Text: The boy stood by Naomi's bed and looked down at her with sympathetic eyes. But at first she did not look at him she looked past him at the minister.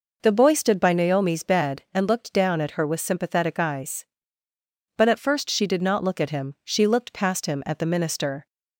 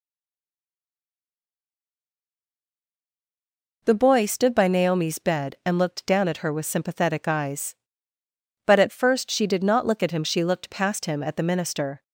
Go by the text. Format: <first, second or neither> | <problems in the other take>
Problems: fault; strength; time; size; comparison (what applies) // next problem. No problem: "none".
first | stays silent before the first word; strong; until 3.8 s; 3.8 s long